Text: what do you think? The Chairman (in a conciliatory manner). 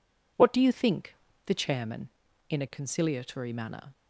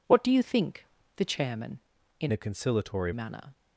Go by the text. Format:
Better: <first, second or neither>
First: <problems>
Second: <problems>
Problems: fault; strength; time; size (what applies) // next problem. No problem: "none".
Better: first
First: none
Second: changes voice from "a" to "conciliatory"; from 2.3 to 3.1 s; 0.8 s long